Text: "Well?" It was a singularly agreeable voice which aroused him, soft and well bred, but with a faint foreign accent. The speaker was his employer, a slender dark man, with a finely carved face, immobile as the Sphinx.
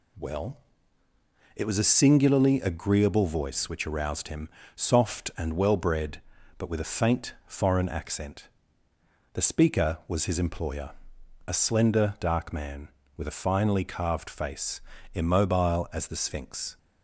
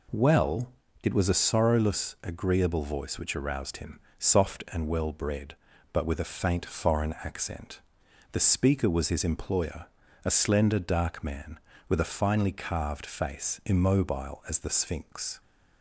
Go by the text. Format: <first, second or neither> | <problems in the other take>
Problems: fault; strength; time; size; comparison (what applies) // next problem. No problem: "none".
first | says "sorrowless" for "singularly"; at 1.4 s